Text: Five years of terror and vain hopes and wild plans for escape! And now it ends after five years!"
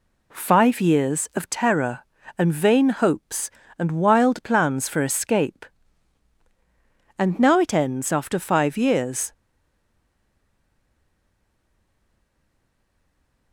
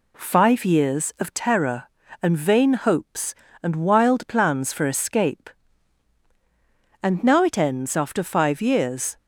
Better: second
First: stays silent after the last word; strong; from 9.3 s on; 4.2 s long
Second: none

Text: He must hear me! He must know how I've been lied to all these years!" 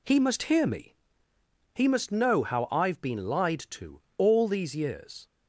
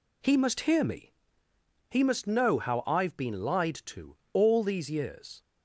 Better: neither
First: pauses between "to" and "all"; slight; at 3.9 s; 0.18 s long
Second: pauses between "to" and "all"; slight; at 4.1 s; 0.18 s long

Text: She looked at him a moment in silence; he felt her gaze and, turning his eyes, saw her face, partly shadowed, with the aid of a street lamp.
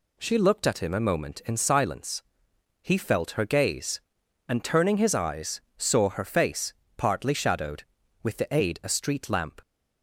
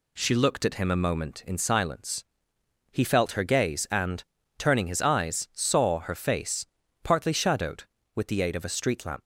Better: second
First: skips "of"; at 8.8 s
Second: none

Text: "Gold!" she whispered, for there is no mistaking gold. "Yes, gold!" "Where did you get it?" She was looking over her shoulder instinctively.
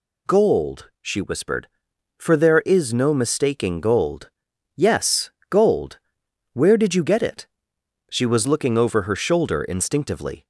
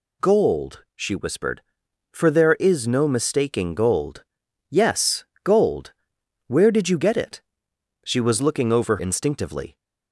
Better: first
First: none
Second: skips "her shoulder"; at 8.9 s

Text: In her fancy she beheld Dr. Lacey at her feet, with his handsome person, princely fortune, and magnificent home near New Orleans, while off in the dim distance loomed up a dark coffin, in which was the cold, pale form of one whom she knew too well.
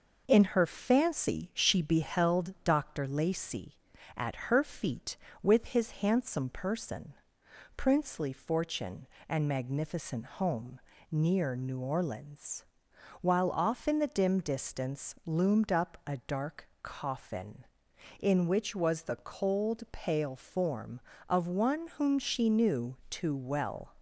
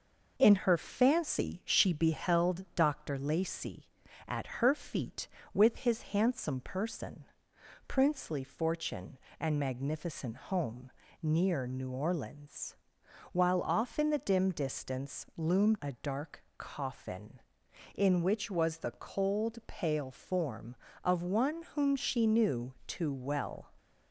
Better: first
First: pauses between "home" and "near"; slight; at 10.7 s; 0.32 s long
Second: pauses between "home" and "near"; slight; at 10.9 s; 0.32 s long // skips "up"; at 15.8 s

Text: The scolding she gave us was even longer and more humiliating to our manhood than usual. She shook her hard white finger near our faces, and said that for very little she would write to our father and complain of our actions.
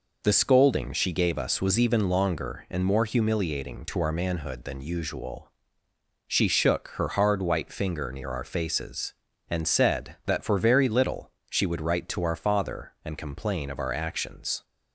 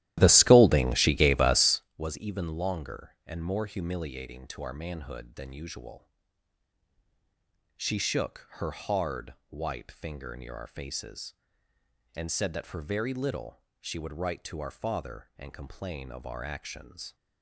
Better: first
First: pauses between "little" and "she"; slight; at 11.2 s; 0.20 s long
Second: starts louder than the rest; strong; until 1.9 s; 14 dB // pauses between "little" and "she"; slight; at 13.6 s; 0.18 s long

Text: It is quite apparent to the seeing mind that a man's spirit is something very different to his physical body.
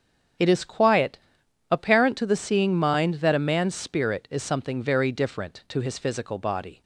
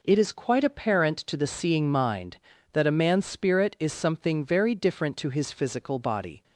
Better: second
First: starts louder than the rest; strong; until 1.9 s; 7.5 dB // says "quiet" for "quite"; at 0.6 s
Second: none

